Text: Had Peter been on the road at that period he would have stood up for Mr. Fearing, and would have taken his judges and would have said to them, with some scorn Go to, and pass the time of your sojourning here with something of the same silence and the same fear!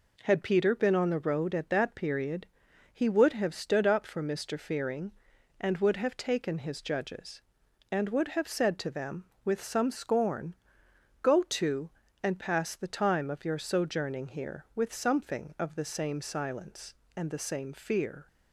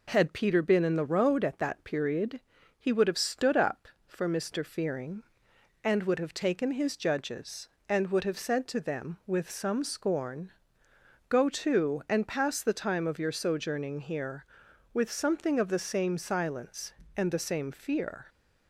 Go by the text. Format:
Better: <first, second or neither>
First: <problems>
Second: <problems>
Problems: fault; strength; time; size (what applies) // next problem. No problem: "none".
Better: first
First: pauses between "period" and "he"; noticeable; at 2.4 s; 0.48 s long // pauses between "scorn" and "Go"; noticeable; at 10.5 s; 0.66 s long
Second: says "in" for "on"; at 0.8 s // pauses between "period" and "he"; at 2.4 s; 0.38 s long // pauses between "scorn" and "Go"; noticeable; at 10.5 s; 0.78 s long